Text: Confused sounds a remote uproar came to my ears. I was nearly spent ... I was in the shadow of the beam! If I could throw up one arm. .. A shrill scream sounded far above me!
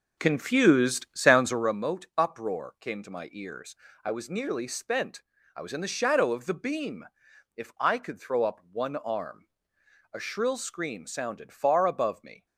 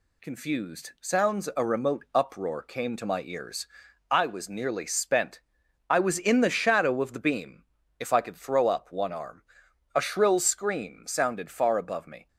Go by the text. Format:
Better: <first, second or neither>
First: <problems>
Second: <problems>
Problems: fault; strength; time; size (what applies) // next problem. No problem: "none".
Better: second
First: starts louder than the rest; noticeable; until 1.8 s; 4.5 dB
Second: none